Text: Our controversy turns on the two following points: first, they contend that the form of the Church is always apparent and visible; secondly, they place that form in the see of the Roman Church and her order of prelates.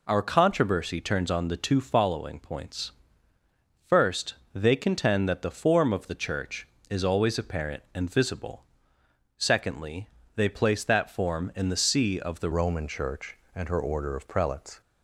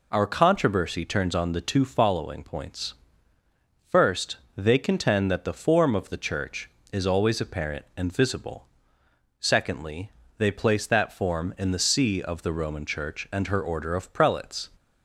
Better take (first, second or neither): second